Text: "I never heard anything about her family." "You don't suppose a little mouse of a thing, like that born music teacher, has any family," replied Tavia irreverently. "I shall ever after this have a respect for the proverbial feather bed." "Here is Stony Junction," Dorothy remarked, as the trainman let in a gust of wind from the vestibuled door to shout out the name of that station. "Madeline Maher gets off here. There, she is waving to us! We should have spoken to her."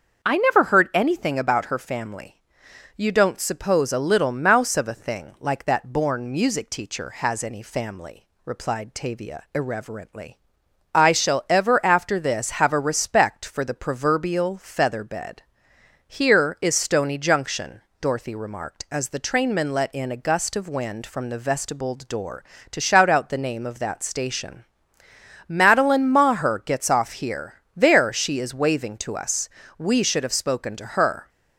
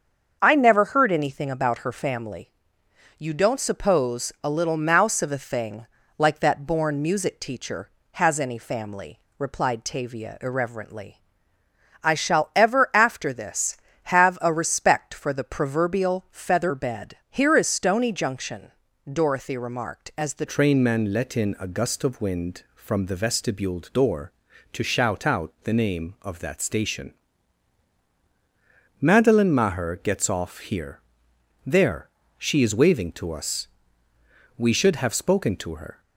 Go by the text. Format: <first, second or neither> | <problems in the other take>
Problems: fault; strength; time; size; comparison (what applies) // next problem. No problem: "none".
first | starts louder than the rest; until 1.4 s; 6.5 dB; also in the first // changes voice at "trainman"; from 20.4 s on; 15.5 s long